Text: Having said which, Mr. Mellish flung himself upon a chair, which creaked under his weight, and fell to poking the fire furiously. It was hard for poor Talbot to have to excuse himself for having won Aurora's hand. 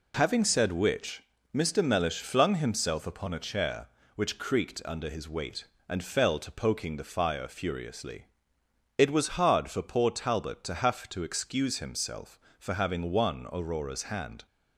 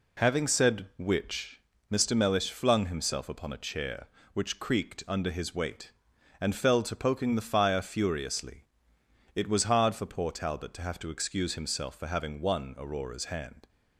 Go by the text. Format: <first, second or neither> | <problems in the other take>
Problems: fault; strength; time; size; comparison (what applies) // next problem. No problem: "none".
neither | none